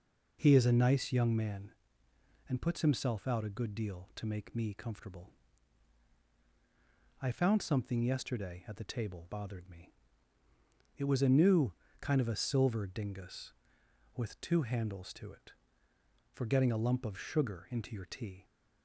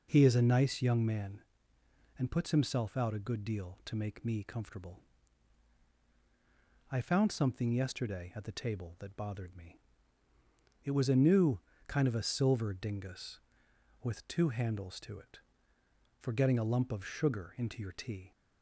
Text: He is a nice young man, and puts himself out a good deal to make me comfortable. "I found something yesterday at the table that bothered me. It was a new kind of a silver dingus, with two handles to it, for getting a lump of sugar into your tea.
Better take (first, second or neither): second